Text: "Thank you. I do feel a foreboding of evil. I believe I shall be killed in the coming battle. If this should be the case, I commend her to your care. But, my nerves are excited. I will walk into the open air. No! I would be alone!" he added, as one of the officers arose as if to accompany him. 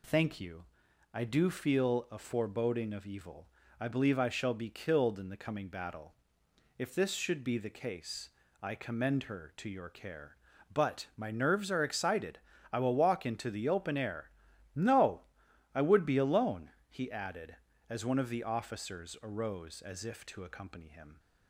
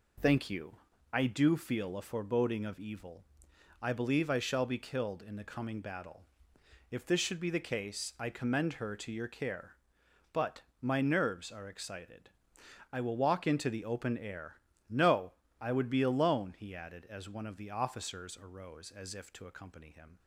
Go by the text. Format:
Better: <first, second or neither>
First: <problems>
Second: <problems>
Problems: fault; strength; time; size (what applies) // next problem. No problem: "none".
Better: neither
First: none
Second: none